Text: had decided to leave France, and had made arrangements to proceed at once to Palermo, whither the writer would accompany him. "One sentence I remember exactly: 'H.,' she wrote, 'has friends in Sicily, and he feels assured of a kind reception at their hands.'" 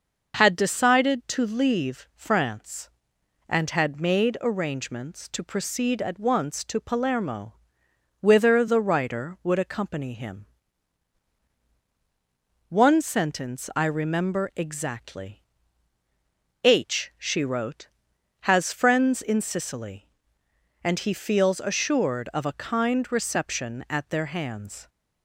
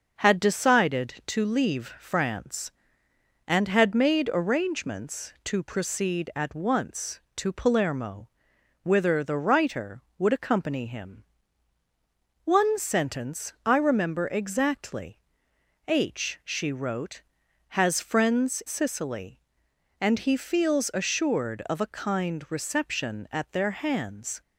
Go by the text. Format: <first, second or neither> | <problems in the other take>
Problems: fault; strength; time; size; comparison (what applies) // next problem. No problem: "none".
first | starts louder than the rest; until 1.2 s; 6.5 dB // skips "in"; at 18.6 s